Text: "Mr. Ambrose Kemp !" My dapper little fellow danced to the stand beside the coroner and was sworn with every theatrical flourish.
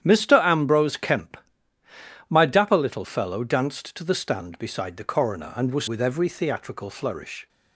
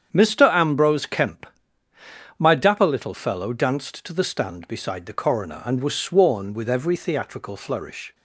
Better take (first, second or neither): second